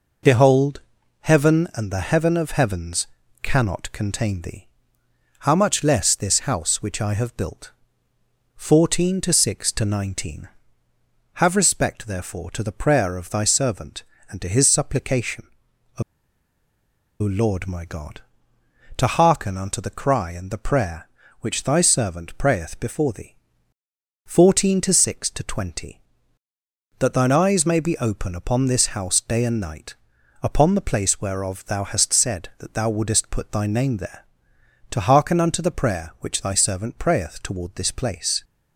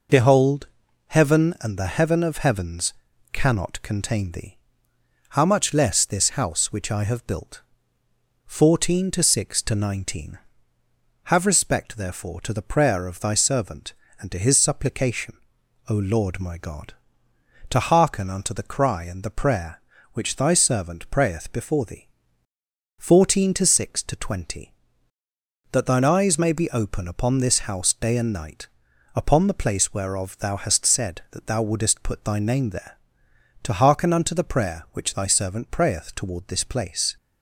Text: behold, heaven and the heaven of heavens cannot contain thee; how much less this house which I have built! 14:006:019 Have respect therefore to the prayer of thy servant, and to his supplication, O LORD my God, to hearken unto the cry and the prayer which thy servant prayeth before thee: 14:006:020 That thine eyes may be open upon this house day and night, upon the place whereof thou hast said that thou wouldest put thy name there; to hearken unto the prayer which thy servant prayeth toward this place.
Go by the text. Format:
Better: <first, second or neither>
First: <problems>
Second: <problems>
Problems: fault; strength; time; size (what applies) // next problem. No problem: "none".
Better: second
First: pauses between "heavens" and "cannot"; slight; at 3.0 s; 0.36 s long // pauses between "O" and "LORD"; at 16.0 s; 1.1 s long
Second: pauses between "heavens" and "cannot"; at 2.9 s; 0.39 s long